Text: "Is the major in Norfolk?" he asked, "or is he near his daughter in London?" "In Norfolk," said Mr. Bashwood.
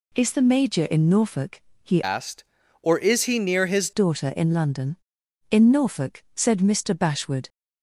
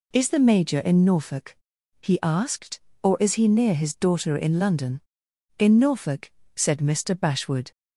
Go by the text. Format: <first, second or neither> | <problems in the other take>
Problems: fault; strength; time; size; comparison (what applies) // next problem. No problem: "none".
second | changes voice from "asked" to "his"; from 2.0 to 3.9 s; 1.9 s long